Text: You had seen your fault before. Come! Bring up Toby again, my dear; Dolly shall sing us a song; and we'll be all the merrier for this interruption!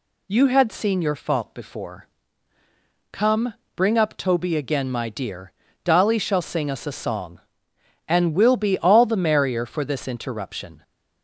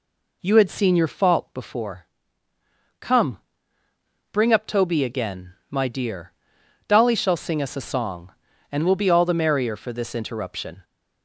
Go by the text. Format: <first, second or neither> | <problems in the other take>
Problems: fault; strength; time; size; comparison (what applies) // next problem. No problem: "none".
neither | none